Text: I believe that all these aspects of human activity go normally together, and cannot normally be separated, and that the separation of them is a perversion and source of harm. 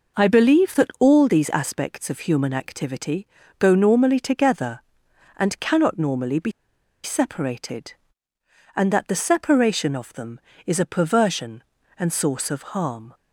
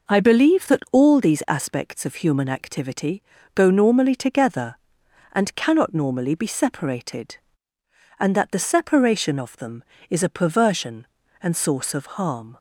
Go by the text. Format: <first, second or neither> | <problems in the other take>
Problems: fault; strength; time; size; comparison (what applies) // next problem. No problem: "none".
second | pauses between "activity" and "go"; slight; at 3.2 s; 0.32 s long; slight in the second // pauses between "be" and "separated"; noticeable; at 6.5 s; 0.52 s long